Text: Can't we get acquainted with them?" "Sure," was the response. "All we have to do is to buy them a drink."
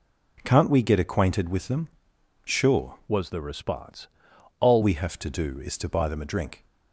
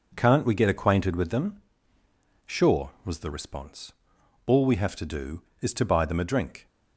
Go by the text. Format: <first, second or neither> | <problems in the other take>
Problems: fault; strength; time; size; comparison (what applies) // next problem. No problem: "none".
second | changes voice from "was" to "All"; from 3.0 to 4.8 s; 1.8 s long